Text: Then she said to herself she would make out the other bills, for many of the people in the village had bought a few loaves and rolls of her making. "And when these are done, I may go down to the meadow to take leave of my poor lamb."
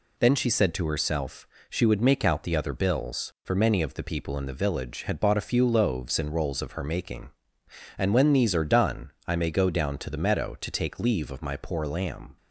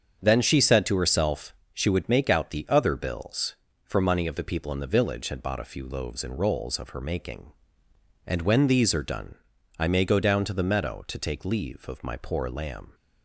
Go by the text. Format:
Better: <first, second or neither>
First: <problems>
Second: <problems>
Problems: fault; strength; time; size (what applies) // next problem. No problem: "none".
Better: first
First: pauses between "herself" and "she"; slight; at 1.4 s; 0.22 s long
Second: starts louder than the rest; strong; until 1.2 s; 7.5 dB // pauses between "herself" and "she"; slight; at 1.5 s; 0.18 s long // says "money" for "many"; at 4.0 s